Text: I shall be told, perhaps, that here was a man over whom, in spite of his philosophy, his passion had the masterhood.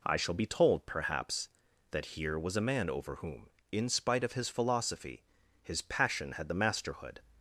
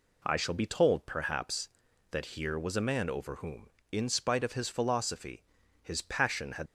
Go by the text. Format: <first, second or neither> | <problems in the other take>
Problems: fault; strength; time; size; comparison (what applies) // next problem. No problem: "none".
first | stops before "the masterhood"; at 6.6 s